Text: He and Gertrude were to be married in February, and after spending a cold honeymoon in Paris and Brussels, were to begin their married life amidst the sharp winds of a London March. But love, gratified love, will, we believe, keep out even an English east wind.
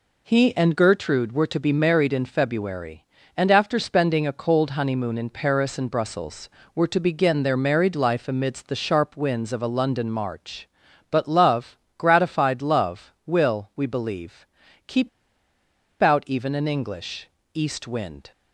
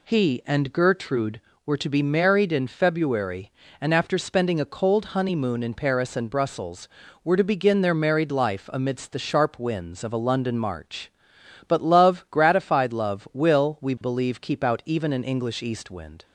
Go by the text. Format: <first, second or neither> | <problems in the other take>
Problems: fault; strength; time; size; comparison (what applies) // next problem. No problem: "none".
second | pauses between "keep" and "out"; noticeable; at 15.0 s; 0.93 s long // pauses between "English" and "east"; slight; at 17.2 s; 0.24 s long